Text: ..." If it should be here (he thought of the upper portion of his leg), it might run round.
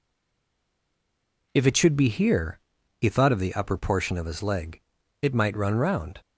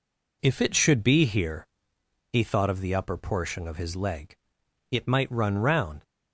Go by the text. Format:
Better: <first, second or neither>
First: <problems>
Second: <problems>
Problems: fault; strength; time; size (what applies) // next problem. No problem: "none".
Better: second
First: stays silent before the first word; noticeable; until 1.5 s; 1.5 s long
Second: none